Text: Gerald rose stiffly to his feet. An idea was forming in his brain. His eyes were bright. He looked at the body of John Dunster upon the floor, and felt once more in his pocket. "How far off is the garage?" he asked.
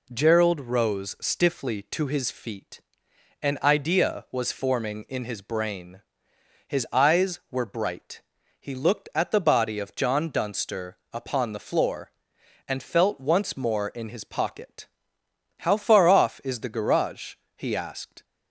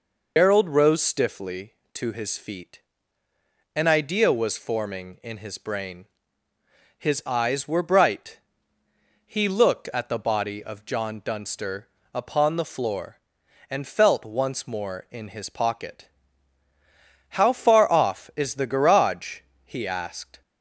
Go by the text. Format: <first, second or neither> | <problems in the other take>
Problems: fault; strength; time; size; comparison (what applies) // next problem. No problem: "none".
first | loses the start of "Gerald"; at 0.3 s; 125 ms // pauses between "Dunster" and "upon"; slight; at 11.8 s; 0.26 s long